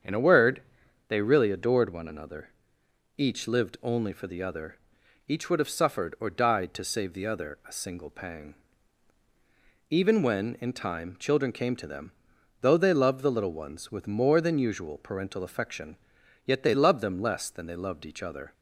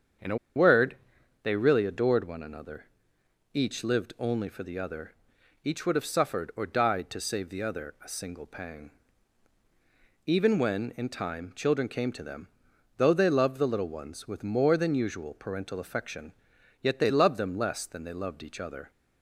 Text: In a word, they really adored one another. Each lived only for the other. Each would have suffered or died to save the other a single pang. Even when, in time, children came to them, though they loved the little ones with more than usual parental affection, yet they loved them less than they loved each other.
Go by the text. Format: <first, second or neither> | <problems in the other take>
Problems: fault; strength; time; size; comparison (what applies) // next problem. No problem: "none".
first | starts louder than the rest; strong; until 1.8 s; 7.5 dB; strong in the first // pauses between "a" and "word"; slight; at 0.3 s; 0.19 s long